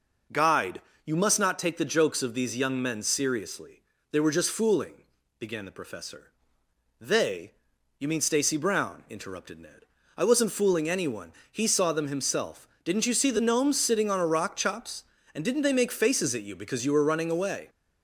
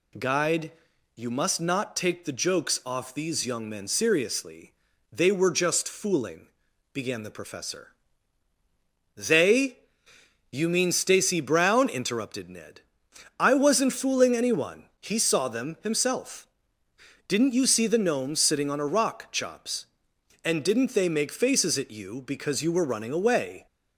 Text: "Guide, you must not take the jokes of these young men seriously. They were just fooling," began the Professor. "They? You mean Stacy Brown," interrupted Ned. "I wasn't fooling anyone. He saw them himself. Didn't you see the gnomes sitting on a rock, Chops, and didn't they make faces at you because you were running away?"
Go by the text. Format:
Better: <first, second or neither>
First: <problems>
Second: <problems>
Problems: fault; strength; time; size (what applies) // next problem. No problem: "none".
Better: first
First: none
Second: says "off" for "of"; at 2.8 s